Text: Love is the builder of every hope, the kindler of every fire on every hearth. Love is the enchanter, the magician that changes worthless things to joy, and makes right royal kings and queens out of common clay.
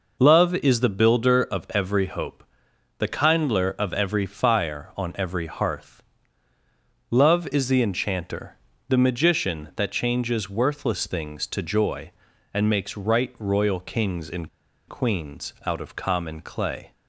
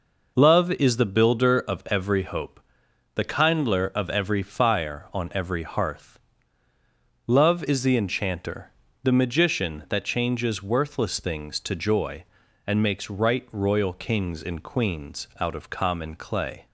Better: second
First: pauses between "and" and "queens"; at 14.4 s; 0.40 s long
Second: none

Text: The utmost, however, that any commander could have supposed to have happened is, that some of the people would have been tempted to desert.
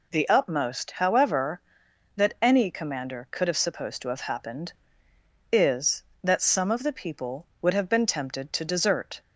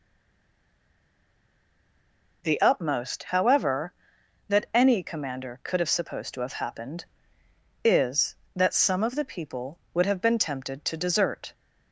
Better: first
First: none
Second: stays silent before the first word; until 2.4 s; 2.4 s long

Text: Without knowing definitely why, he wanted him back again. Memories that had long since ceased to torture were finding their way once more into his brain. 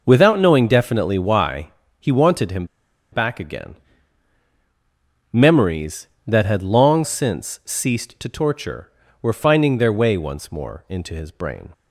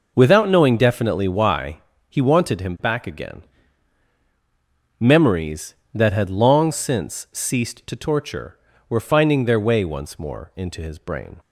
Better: second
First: pauses between "him" and "back"; noticeable; at 2.6 s; 0.47 s long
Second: none

